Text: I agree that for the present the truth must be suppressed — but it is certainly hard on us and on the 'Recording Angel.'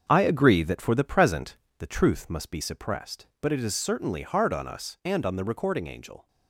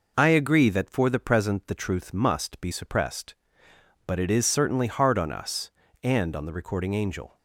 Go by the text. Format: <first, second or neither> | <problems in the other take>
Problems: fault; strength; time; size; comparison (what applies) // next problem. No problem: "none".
second | gets quieter; strong; throughout; 7.5 dB // pauses between "present" and "the"; slight; at 1.5 s; 0.22 s long